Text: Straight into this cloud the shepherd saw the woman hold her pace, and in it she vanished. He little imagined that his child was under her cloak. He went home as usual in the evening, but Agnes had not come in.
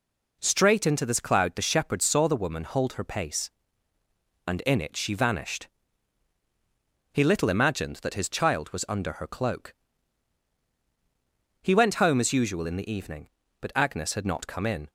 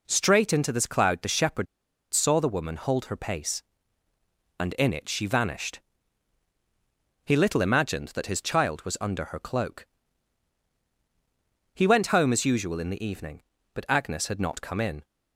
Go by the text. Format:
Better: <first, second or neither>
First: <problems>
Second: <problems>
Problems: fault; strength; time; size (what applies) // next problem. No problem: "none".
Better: first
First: none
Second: pauses between "shepherd" and "saw"; noticeable; at 1.6 s; 0.47 s long